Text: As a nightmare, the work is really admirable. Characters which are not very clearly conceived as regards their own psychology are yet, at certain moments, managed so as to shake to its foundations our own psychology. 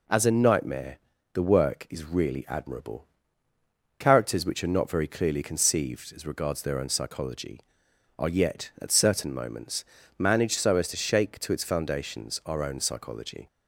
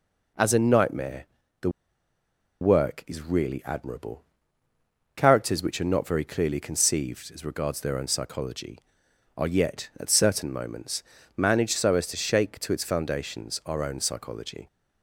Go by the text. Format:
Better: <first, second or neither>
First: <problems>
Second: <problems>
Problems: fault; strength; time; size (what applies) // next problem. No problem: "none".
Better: first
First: none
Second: pauses between "the" and "work"; noticeable; at 1.6 s; 0.91 s long